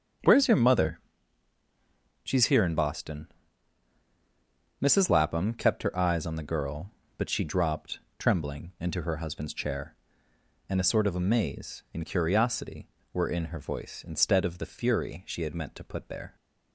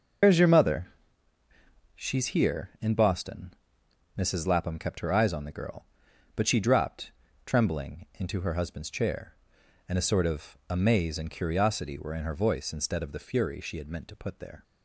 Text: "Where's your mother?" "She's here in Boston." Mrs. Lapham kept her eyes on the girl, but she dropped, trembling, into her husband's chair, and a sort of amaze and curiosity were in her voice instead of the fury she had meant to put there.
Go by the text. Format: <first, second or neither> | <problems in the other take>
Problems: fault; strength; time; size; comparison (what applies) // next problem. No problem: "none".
first | loses the start of "Where's"; at 0.2 s; 120 ms // starts louder than the rest; noticeable; until 2.2 s; 6 dB; also in the first